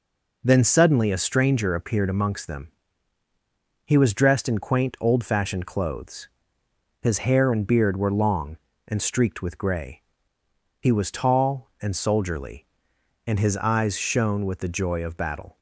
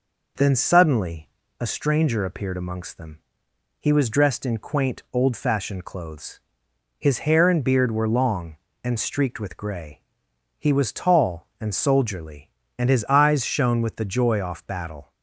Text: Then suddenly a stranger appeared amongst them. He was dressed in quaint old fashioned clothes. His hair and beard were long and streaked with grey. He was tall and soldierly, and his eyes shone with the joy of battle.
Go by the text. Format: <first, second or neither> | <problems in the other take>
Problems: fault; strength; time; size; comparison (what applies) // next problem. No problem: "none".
first | pauses between "suddenly" and "a"; slight; at 1.2 s; 0.30 s long // says "off" for "of"; at 14.4 s